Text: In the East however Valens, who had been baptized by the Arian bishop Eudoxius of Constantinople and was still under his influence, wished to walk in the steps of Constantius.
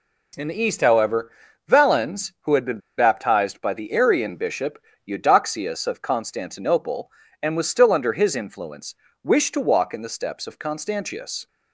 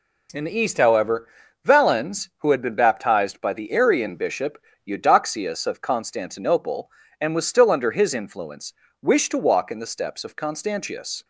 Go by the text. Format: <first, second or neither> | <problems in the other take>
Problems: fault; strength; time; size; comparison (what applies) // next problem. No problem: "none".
second | pauses between "however" and "Valens"; at 1.2 s; 0.38 s long; also in the second // pauses between "been" and "baptized"; slight; at 2.7 s; 0.17 s long // pauses between "bishop" and "Eudoxius"; slight; at 4.7 s; 0.28 s long; slight in the second